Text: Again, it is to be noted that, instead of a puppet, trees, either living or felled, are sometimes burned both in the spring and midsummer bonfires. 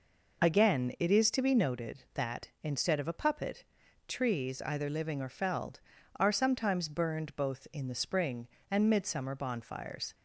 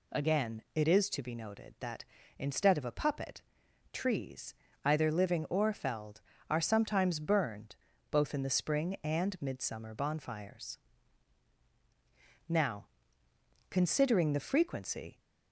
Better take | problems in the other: first | pauses between "burned" and "both"; slight; at 7.7 s; 0.36 s long // goes on to say "Now considering the frequency"; strong; from 12.5 s on; 2.6 s long

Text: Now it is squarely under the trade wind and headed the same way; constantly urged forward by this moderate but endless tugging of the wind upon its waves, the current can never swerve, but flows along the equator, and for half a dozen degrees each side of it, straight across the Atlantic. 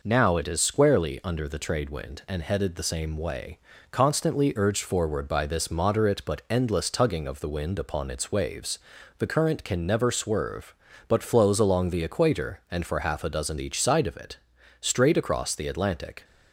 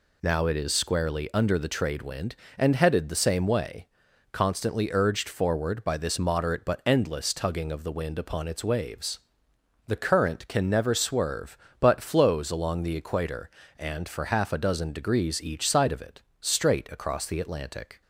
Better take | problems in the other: second | skips "degrees"; at 13.5 s

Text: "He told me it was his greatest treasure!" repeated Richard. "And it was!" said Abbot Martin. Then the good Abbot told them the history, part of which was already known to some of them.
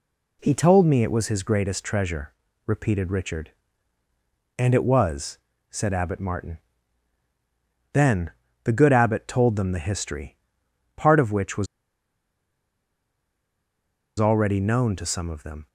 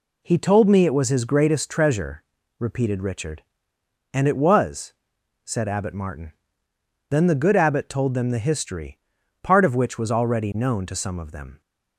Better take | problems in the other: second | pauses between "Then" and "the"; slight; at 8.3 s; 0.34 s long // pauses between "was" and "already"; strong; at 11.6 s; 2.5 s long

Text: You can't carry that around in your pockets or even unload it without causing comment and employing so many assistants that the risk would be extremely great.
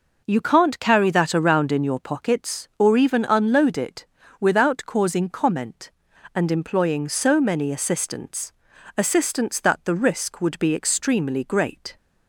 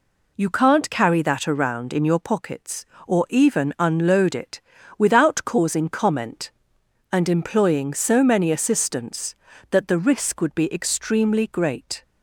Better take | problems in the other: second | pauses between "it" and "without"; slight; at 4.0 s; 0.34 s long; also in the second // says "assistants" twice; at 8.9 s

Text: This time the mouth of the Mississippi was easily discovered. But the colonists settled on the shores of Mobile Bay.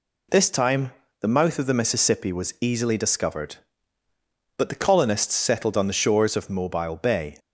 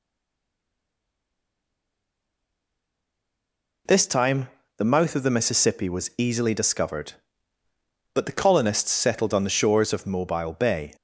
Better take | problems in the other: first | stays silent before the first word; strong; until 3.8 s; 3.8 s long // pauses between "time" and "the"; slight; at 4.4 s; 0.30 s long; slight in the first

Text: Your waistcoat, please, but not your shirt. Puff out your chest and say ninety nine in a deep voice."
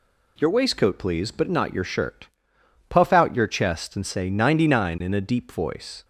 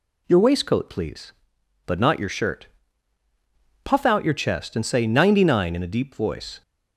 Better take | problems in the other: neither | none

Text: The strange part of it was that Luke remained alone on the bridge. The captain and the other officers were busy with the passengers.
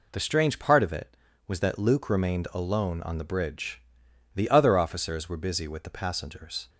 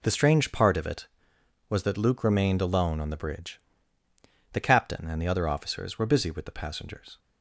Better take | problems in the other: second | skips "captain and the"; at 4.4 s

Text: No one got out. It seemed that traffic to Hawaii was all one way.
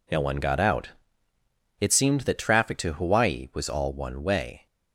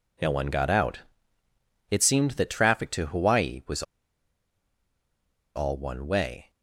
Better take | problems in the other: first | pauses between "was" and "all"; strong; at 3.8 s; 1.7 s long

